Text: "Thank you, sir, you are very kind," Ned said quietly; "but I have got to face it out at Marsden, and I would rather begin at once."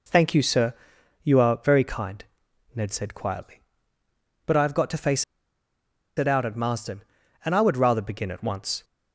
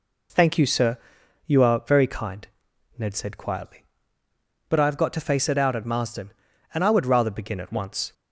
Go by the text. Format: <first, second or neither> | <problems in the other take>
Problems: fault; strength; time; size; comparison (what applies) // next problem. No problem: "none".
second | pauses between "face" and "it"; noticeable; at 5.2 s; 0.94 s long